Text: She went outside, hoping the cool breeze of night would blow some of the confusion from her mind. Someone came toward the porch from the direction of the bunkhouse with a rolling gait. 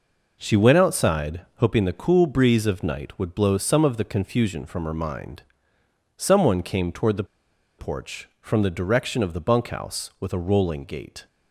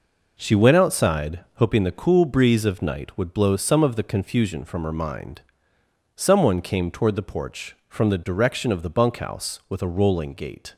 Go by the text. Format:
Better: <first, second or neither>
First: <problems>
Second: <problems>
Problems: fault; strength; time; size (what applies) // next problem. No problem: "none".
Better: second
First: pauses between "the" and "porch"; noticeable; at 7.2 s; 0.55 s long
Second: none